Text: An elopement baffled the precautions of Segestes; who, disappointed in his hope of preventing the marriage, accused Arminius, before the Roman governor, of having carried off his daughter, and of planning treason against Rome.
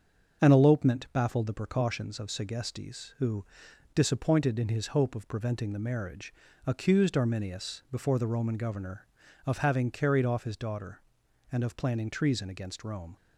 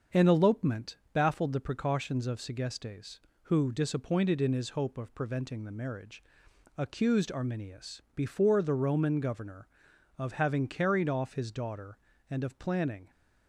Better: first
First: starts louder than the rest; until 1.5 s; 7 dB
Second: starts louder than the rest; until 1.2 s; 6.5 dB // pauses between "elopement" and "baffled"; slight; at 0.9 s; 0.16 s long // stops before "treason against Rome"; at 13.1 s

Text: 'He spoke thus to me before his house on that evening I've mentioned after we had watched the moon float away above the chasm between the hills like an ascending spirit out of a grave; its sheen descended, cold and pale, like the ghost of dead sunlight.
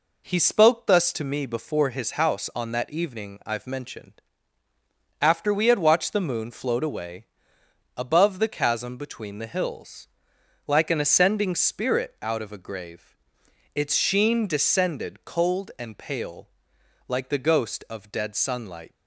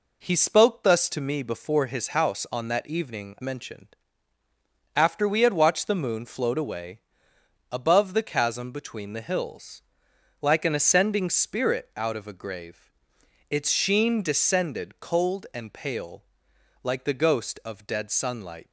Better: first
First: pauses between "mentioned" and "after"; noticeable; at 4.2 s; 0.98 s long // pauses between "away" and "above"; noticeable; at 7.2 s; 0.68 s long // pauses between "hills" and "like"; noticeable; at 10.0 s; 0.60 s long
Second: skips "I've"; at 3.3 s // pauses between "mentioned" and "after"; noticeable; at 3.9 s; 0.98 s long // pauses between "away" and "above"; noticeable; at 7.0 s; 0.68 s long // pauses between "hills" and "like"; noticeable; at 9.8 s; 0.60 s long

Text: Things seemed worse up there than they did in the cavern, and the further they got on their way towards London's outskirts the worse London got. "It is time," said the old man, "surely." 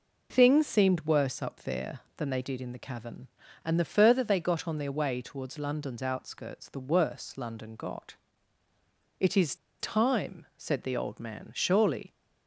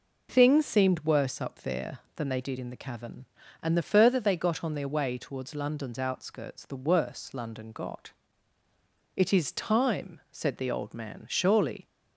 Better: second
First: pauses between "is" and "time"; slight; at 9.5 s; 0.24 s long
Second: none

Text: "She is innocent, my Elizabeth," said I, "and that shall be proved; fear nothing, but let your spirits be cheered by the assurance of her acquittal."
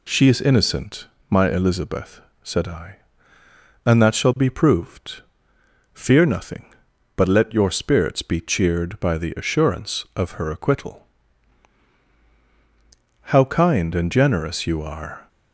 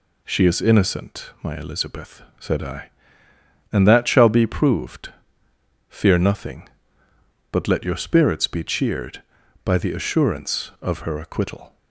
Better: second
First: goes on to say "How kind and generous you are"; strong; from 13.2 s on; 2.0 s long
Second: none

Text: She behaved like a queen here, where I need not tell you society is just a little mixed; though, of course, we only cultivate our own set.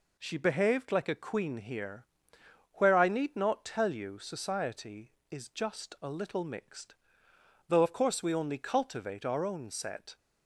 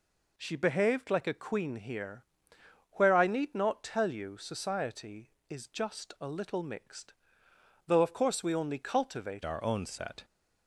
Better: first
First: none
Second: changes voice at "our"; from 9.4 s on; 0.8 s long

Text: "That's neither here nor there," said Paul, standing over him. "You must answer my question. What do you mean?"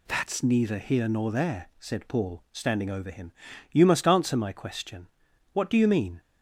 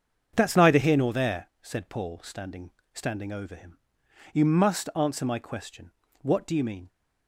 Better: first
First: none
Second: starts louder than the rest; until 1.3 s; 7 dB // says "standing" twice; at 2.9 s

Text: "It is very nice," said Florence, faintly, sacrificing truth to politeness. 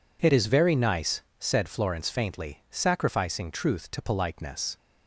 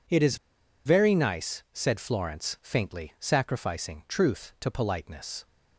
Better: first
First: none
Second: pauses between "is" and "very"; noticeable; at 0.3 s; 0.48 s long

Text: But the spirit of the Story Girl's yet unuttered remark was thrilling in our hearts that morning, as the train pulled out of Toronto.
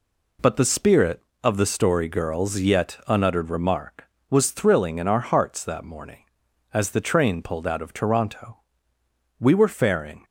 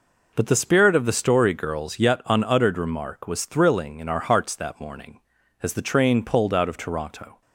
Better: second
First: goes on to say "We were faring"; noticeable; from 9.3 s on; 0.86 s long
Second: none

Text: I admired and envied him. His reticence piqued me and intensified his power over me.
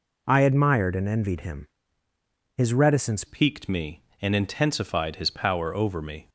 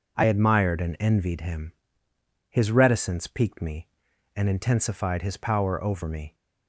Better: second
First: changes voice at "piqued"; from 3.2 s on; 3.0 s long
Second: none

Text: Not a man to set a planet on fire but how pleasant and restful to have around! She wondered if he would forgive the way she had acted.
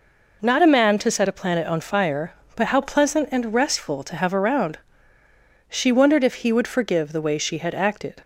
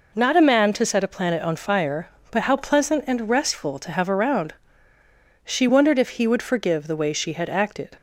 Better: neither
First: none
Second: none

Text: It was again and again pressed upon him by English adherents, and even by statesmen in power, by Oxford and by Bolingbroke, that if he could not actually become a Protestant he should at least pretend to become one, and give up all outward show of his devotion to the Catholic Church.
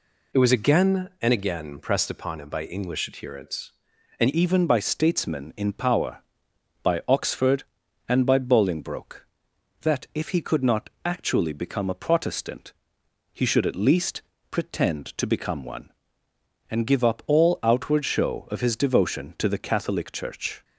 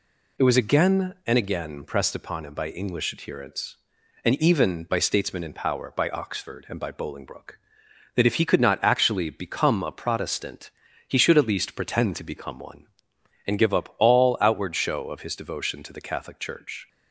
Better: second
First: changes voice at "even"; from 4.3 s on; 16.3 s long // pauses between "not" and "actually"; slight; at 10.8 s; 0.16 s long // pauses between "Protestant" and "he"; noticeable; at 12.7 s; 0.60 s long // pauses between "least" and "pretend"; slight; at 14.2 s; 0.30 s long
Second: pauses between "Protestant" and "he"; at 10.7 s; 0.37 s long

